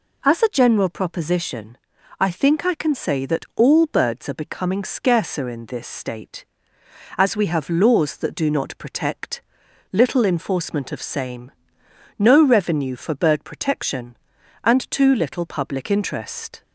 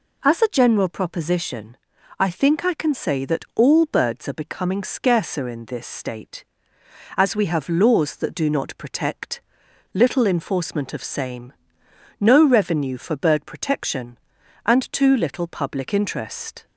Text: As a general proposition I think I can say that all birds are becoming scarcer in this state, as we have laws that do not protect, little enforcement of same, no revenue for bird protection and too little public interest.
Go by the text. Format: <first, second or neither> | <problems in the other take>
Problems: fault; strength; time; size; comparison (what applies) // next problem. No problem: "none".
neither | pauses between "proposition" and "I"; the same in both